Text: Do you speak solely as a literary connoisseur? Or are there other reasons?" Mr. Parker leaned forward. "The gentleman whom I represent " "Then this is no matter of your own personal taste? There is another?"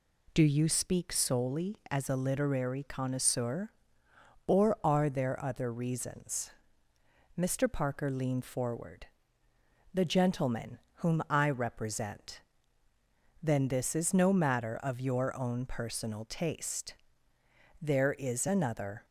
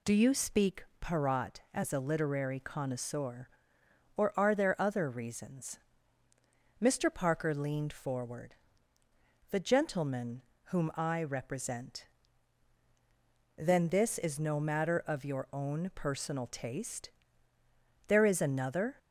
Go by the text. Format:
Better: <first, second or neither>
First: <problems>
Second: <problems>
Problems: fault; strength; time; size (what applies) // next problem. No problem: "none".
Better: first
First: pauses between "gentleman" and "whom"; slight; at 10.7 s; 0.20 s long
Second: says "parat" for "solely"; at 1.0 s // pauses between "gentleman" and "whom"; slight; at 10.4 s; 0.30 s long